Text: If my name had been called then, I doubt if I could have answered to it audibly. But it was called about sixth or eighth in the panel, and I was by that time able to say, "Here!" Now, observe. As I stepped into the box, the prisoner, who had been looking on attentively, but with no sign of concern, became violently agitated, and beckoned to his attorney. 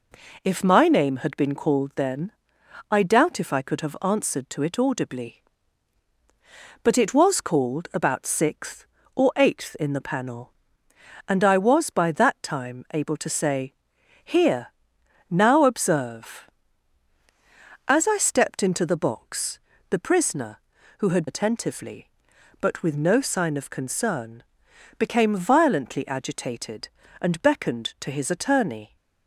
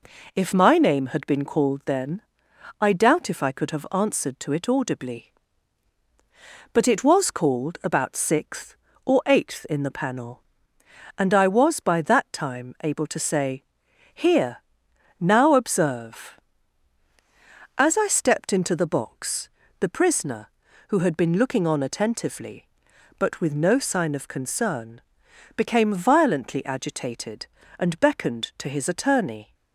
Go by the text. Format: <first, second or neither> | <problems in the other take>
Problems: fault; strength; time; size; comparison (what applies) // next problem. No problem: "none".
second | skips "been looking on"; at 21.2 s